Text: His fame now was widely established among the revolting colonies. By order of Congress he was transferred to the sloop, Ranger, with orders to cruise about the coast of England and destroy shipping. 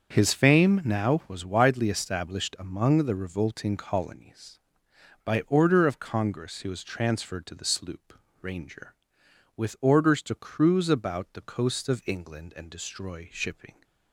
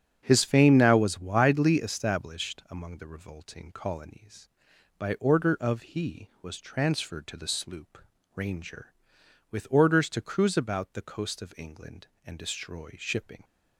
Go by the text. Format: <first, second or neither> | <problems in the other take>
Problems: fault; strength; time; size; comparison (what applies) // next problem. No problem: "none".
first | starts louder than the rest; strong; until 1.2 s; 8.5 dB; also in the first // skips "Congress"; at 5.8 s